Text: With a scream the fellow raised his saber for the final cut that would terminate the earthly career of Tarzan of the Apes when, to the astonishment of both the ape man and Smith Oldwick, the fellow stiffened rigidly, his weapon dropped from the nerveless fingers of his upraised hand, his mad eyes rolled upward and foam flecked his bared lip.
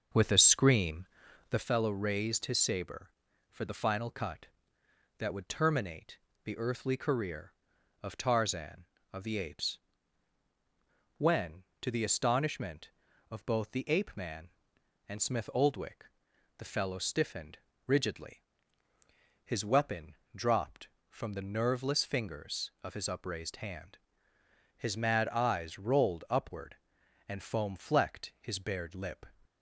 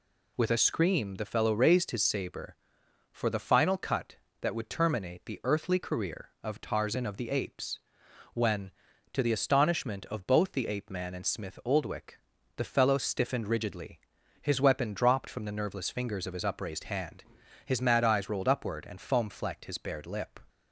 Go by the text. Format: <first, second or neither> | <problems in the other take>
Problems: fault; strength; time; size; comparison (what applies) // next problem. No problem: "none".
second | starts louder than the rest; until 1.7 s; 6.5 dB // pauses between "scream" and "the"; noticeable; at 1.0 s; 0.46 s long // pauses between "terminate" and "the"; slight; at 6.1 s; 0.26 s long // pauses between "Apes" and "when"; strong; at 9.7 s; 1.4 s long; noticeable in the second // pauses between "stiffened" and "rigidly"; slight; at 17.5 s; 0.28 s long // pauses between "weapon" and "dropped"; slight; at 20.1 s; 0.20 s long